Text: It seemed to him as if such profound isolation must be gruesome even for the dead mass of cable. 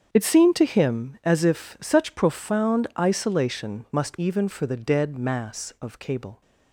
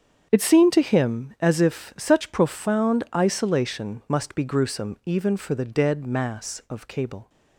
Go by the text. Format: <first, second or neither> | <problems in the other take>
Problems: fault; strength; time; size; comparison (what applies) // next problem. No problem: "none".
second | starts louder than the rest; strong; until 1.1 s; 7.5 dB; strong in the second // skips "be gruesome"; at 4.1 s